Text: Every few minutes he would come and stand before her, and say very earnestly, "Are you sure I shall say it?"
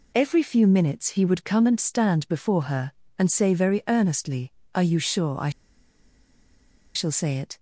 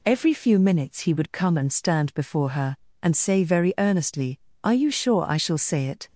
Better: second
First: pauses between "I" and "shall"; strong; at 5.5 s; 1.4 s long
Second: none

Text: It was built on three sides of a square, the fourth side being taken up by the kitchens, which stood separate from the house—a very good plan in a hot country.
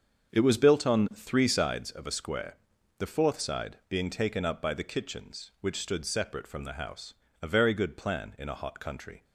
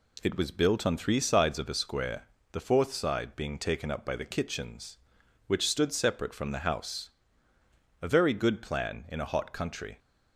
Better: second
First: starts louder than the rest; until 1.9 s; 7 dB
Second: none

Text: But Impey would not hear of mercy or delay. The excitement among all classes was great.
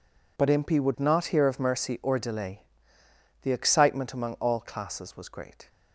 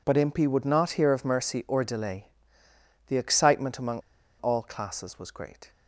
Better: first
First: none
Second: pauses between "among" and "all"; at 3.9 s; 0.39 s long

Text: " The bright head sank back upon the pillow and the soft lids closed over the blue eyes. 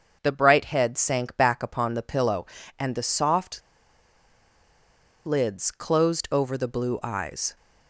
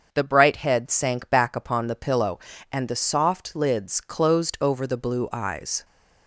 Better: second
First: starts louder than the rest; until 1.2 s; 6.5 dB // pauses between "soft" and "lids"; strong; at 3.6 s; 1.6 s long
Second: starts louder than the rest; until 1.1 s; 6.5 dB

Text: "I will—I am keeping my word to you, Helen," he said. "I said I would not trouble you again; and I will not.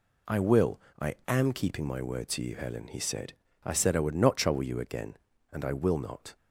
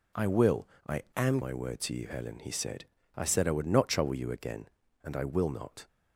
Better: first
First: none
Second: skips "keeping"; at 1.4 s

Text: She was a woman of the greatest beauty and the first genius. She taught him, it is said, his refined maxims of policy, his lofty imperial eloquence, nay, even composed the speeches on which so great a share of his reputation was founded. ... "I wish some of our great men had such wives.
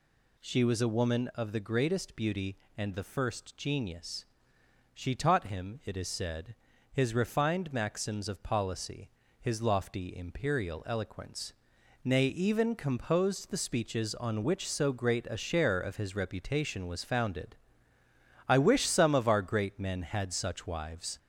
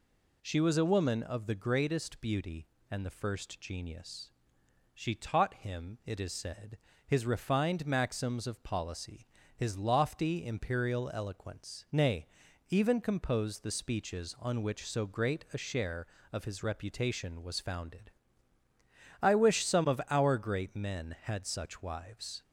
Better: second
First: gets louder; throughout; 4 dB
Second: none

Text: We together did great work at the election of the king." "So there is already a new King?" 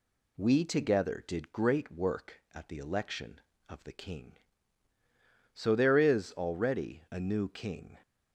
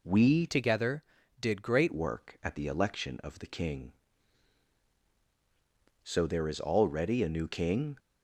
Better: first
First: none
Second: changes voice from "together" to "great"; from 0.4 to 1.9 s; 1.5 s long

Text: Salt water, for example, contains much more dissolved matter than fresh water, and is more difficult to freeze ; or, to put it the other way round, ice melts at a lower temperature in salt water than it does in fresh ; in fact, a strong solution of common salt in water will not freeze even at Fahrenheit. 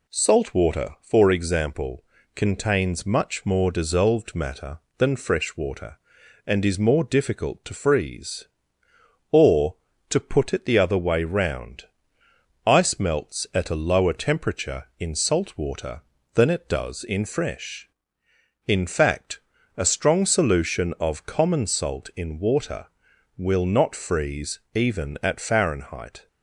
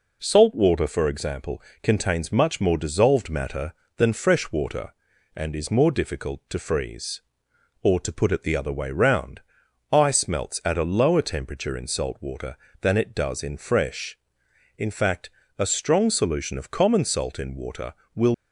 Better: first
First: none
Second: stops before "not freeze even at Fahrenheit"; at 18.3 s

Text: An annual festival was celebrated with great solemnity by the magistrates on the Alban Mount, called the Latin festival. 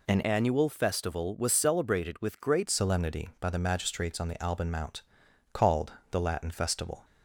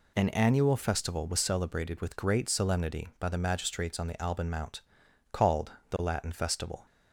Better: second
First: changes voice from "annual" to "great"; from 0.2 to 2.6 s; 2.4 s long // pauses between "called" and "the"; slight; at 5.9 s; 0.18 s long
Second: pauses between "called" and "the"; slight; at 5.7 s; 0.18 s long

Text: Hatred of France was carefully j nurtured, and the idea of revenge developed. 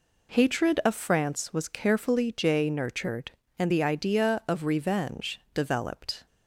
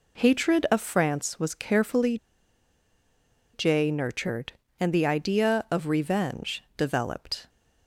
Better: first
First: none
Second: pauses between "carefully" and "j"; strong; at 2.1 s; 1.3 s long

